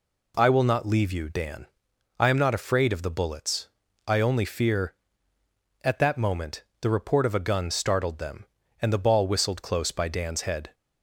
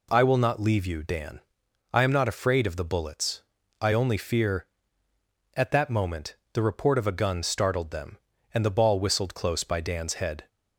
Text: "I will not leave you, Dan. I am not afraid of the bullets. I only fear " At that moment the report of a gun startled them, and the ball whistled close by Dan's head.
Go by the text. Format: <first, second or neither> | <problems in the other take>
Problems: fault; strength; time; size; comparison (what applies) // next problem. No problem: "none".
neither | pauses between "moment" and "the"; slight; the same in both